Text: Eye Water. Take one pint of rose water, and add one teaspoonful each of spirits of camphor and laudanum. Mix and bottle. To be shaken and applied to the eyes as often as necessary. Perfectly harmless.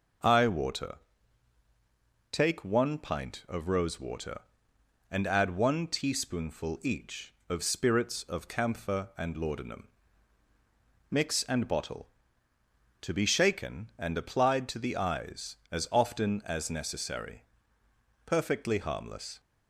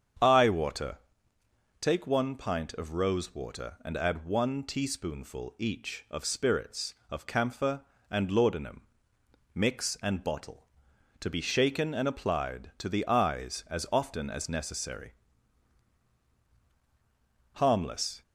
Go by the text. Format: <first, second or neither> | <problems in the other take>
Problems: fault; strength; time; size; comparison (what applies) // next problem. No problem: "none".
first | starts louder than the rest; strong; until 2.0 s; 8 dB // skips "Perfectly"; at 16.3 s